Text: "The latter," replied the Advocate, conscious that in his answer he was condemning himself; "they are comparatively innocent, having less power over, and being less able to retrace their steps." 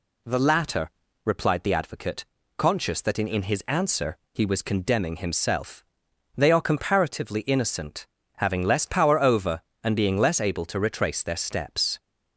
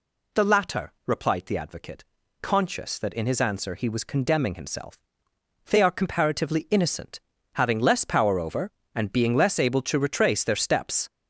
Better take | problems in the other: second | says "in" twice; at 3.2 s // pauses between "answer" and "he"; slight; at 4.1 s; 0.16 s long

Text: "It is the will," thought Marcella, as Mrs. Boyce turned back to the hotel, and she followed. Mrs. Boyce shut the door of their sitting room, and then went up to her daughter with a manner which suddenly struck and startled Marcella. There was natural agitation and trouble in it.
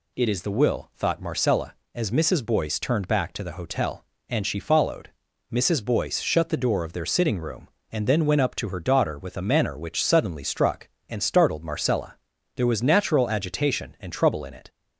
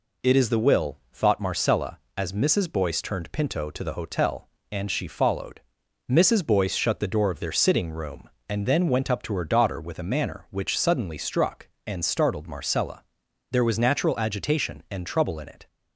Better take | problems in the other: first | says "pinto" for "back"; at 3.3 s

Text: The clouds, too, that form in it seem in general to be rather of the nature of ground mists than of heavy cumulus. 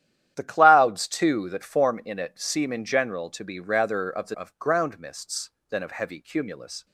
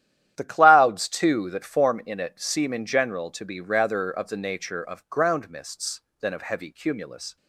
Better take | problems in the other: second | starts louder than the rest; strong; until 1.3 s; 11 dB; strong in the second // skips "nature"; at 4.3 s

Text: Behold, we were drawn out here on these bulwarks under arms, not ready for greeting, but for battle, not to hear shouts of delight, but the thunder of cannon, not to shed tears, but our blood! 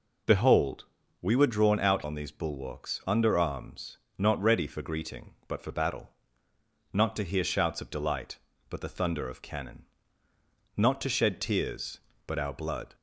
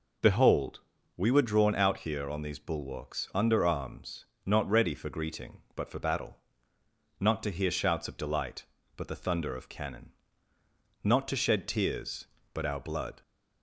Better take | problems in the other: second | skips "here"; at 2.0 s

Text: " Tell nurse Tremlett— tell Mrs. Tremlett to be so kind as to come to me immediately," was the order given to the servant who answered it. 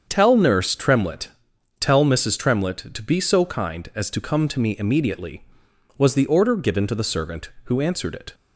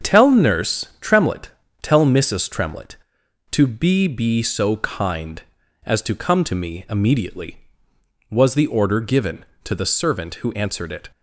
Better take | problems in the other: first | starts louder than the rest; strong; until 1.1 s; 7.5 dB; also in the first // says "be" twice; at 4.0 s

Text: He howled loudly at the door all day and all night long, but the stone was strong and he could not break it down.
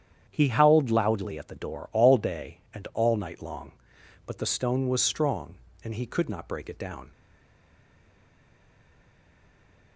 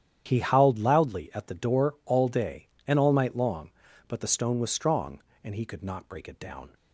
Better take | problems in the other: second | starts louder than the rest; strong; until 1.3 s; 9 dB; strong in the second // stays silent after the last word; strong; from 7.1 s on; 2.8 s long

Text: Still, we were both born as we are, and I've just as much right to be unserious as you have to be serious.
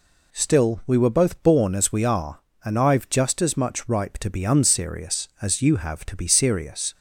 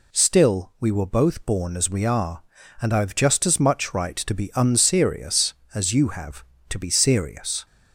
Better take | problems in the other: second | says "ripe" for "right"; at 3.8 s

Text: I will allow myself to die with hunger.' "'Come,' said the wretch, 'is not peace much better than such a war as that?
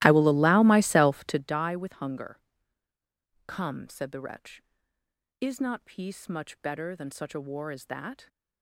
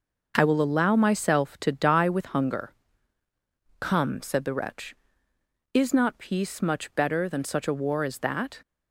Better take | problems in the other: second | starts louder than the rest; strong; until 1.5 s; 16.5 dB

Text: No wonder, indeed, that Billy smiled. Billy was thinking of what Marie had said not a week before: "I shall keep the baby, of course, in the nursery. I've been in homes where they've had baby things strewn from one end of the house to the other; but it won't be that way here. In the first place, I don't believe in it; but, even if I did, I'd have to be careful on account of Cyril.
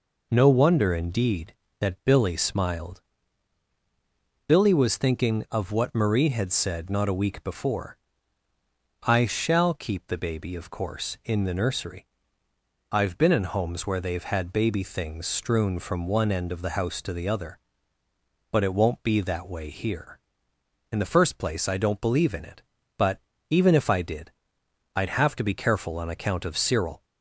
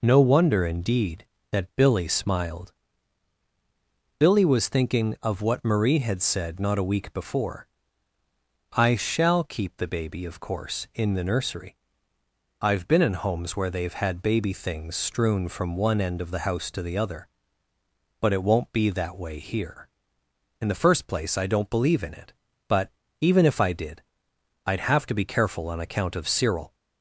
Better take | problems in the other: neither | none

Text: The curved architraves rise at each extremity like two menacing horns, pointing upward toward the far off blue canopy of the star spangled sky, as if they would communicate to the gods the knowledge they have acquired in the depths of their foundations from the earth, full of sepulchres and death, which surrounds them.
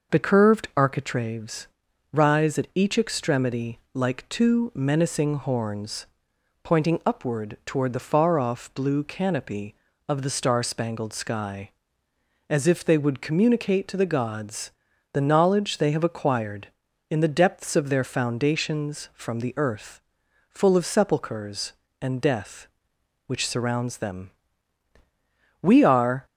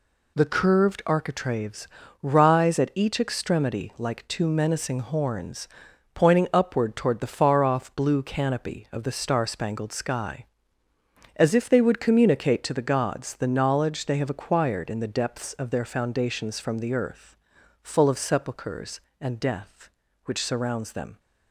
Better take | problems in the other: second | pauses between "architraves" and "rise"; at 1.6 s; 0.44 s long; slight in the second // pauses between "extremity" and "like"; slight; at 3.7 s; 0.16 s long // pauses between "gods" and "the"; at 14.7 s; 0.42 s long // goes on to say "We are"; noticeable; from 25.6 s on; 0.64 s long

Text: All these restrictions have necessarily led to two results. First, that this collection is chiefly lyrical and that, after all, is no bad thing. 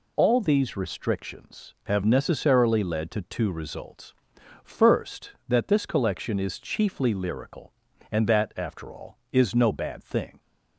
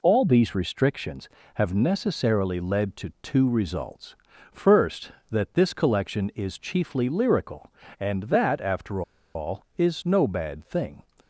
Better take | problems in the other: first | pauses between "after" and "all"; slight; at 9.0 s; 0.33 s long

